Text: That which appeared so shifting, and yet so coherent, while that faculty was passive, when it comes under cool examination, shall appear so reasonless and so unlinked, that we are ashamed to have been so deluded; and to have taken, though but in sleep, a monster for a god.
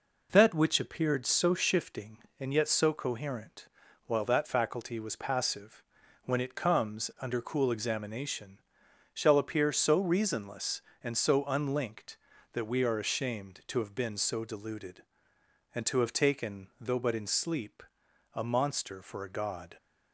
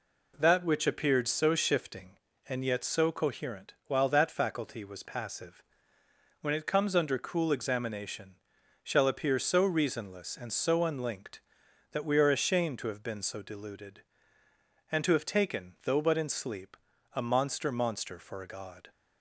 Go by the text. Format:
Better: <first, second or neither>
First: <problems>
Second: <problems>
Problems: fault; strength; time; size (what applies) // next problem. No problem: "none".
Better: first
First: none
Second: says "monster" twice; at 17.6 s